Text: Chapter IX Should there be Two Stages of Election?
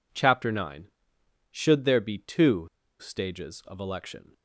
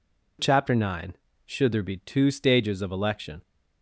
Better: second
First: pauses between "Two" and "Stages"; slight; at 2.6 s; 0.31 s long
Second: none

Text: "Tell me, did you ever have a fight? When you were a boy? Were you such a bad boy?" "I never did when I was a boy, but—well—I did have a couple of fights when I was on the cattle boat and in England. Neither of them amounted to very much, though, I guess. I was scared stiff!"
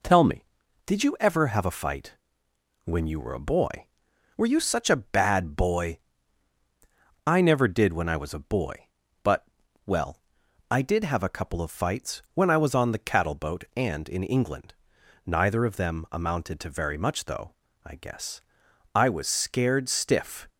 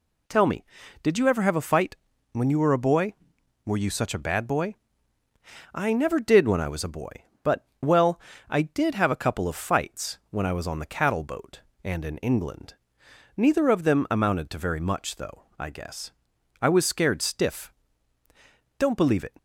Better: first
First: none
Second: goes on to say "Don't believe it"; from 18.7 s on; 0.56 s long

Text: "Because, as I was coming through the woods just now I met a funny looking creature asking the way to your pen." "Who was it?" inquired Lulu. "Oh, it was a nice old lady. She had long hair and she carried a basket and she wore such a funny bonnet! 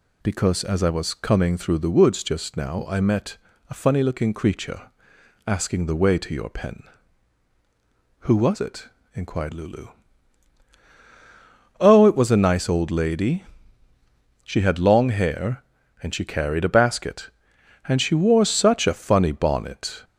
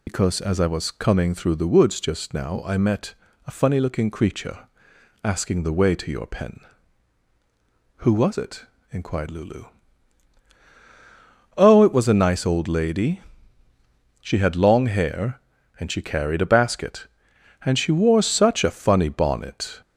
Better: first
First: pauses between "met" and "a"; slight; at 3.3 s; 0.32 s long // pauses between "creature" and "asking"; noticeable; at 4.8 s; 0.58 s long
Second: loses the start of "Because"; at 0.0 s; 80 ms // pauses between "met" and "a"; slight; at 3.1 s; 0.32 s long // pauses between "creature" and "asking"; noticeable; at 4.6 s; 0.58 s long

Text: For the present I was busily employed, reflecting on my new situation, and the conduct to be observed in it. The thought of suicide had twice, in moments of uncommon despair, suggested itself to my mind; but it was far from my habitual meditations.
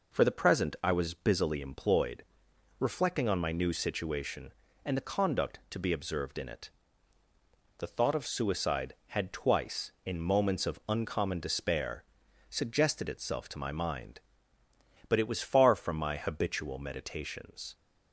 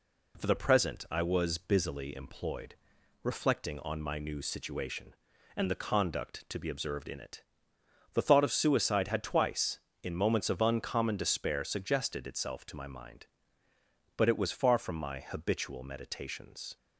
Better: neither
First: none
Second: none

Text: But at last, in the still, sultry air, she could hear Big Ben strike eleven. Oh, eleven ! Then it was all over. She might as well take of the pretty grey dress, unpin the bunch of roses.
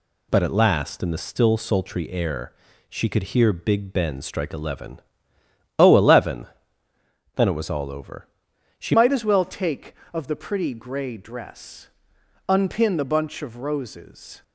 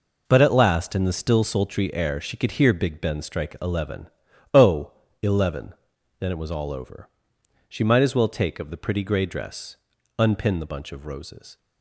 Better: second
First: changes voice at "might"; from 8.9 s on; 5.5 s long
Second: none

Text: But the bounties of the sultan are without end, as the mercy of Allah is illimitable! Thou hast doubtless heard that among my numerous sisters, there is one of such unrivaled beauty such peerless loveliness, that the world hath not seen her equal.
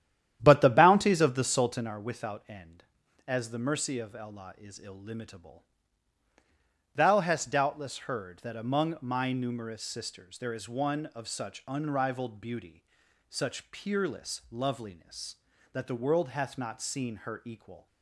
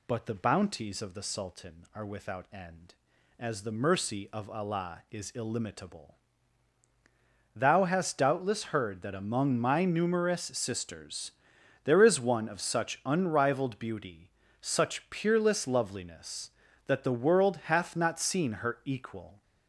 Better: second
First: starts louder than the rest; strong; until 1.9 s; 11 dB // pauses between "beauty" and "such"; noticeable; at 12.8 s; 0.48 s long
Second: pauses between "beauty" and "such"; slight; at 14.2 s; 0.36 s long

